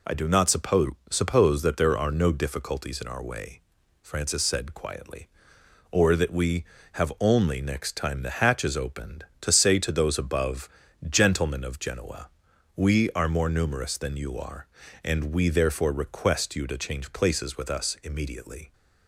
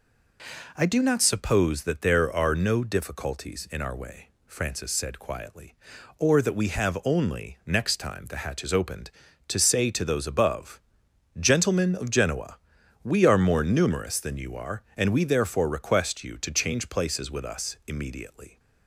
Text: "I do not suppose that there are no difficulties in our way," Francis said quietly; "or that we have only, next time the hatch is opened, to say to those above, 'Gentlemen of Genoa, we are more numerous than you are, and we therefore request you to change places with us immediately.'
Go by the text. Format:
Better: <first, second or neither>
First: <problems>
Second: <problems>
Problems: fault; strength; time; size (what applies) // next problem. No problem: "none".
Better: second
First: says "suppose" twice; at 1.1 s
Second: none